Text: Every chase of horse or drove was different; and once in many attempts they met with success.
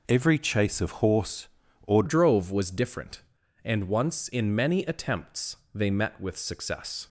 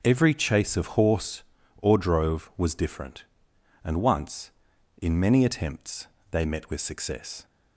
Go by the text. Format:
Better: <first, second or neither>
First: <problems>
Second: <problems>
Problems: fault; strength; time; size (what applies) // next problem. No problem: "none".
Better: second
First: changes voice at "drove"; from 2.0 s on; 5.0 s long // pauses between "attempts" and "they"; slight; at 5.5 s; 0.18 s long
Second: pauses between "attempts" and "they"; slight; at 6.0 s; 0.24 s long